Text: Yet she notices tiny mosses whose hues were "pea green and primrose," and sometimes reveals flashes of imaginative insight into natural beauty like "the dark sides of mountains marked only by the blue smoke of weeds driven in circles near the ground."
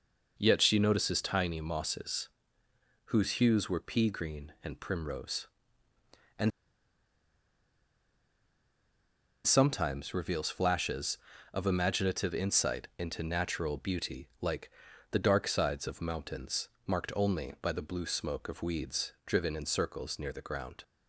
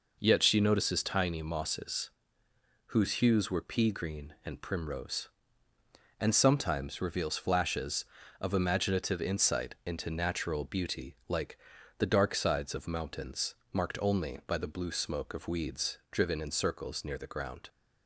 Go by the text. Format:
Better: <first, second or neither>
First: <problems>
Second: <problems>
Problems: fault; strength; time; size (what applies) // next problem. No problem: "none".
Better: second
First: pauses between "mosses" and "whose"; noticeable; at 2.2 s; 0.82 s long // pauses between "and" and "sometimes"; strong; at 6.5 s; 2.9 s long // pauses between "like" and "the"; at 14.6 s; 0.44 s long // pauses between "mountains" and "marked"; slight; at 16.6 s; 0.20 s long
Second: pauses between "mosses" and "whose"; noticeable; at 2.0 s; 0.82 s long // pauses between "like" and "the"; at 11.5 s; 0.44 s long // pauses between "mountains" and "marked"; slight; at 13.5 s; 0.20 s long